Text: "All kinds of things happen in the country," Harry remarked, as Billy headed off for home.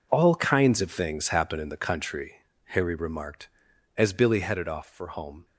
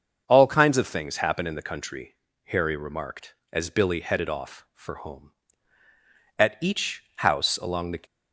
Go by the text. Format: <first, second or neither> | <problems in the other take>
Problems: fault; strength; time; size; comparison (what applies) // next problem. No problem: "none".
first | starts louder than the rest; until 1.2 s; 6.5 dB // goes on to say "At each house along the"; from 6.3 s on; 1.6 s long